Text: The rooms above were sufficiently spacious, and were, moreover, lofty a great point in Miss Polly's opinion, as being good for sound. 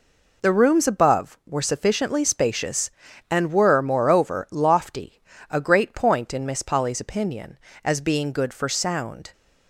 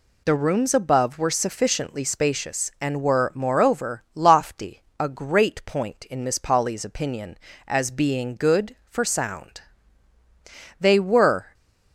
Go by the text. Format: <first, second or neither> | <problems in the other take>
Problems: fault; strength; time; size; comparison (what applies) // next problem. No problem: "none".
first | pauses between "lofty" and "a"; slight; at 4.8 s; 0.20 s long; slight in the first // goes on to say "They were"; noticeable; from 10.7 s on; 0.76 s long